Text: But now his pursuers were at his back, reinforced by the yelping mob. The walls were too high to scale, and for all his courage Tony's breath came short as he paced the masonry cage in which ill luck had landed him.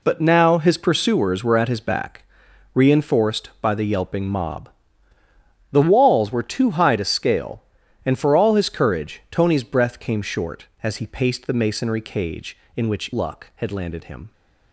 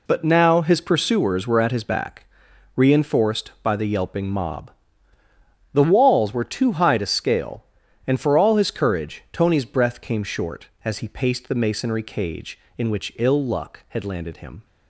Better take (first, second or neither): second